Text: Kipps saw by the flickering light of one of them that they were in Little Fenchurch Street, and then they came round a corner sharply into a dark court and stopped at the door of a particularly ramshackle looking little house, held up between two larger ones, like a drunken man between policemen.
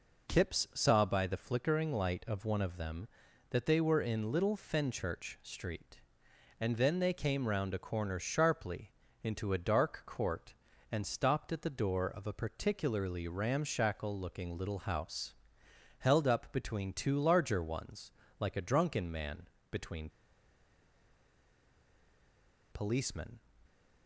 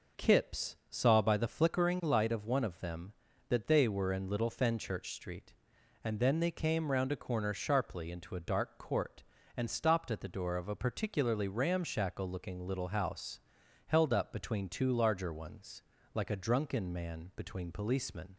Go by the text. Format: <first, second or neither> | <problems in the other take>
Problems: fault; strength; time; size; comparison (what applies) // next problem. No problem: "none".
second | pauses between "sharply" and "into"; slight; at 8.9 s; 0.30 s long // pauses between "man" and "between"; slight; at 19.4 s; 0.22 s long // pauses between "between" and "policemen"; strong; at 20.0 s; 2.6 s long